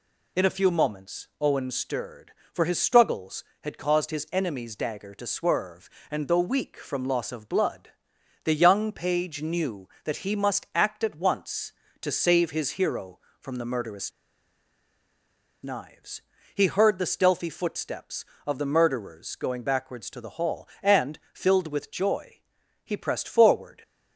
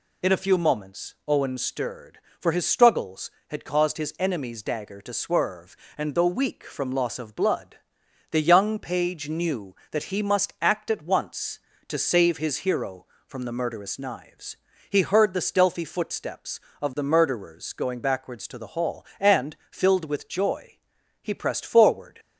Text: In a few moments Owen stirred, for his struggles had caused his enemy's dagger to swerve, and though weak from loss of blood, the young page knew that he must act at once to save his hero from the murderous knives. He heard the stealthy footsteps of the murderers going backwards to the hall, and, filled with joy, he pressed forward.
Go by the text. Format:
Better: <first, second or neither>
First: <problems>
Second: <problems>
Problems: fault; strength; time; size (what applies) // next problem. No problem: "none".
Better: second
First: pauses between "murderous" and "knives"; strong; at 14.1 s; 1.5 s long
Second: none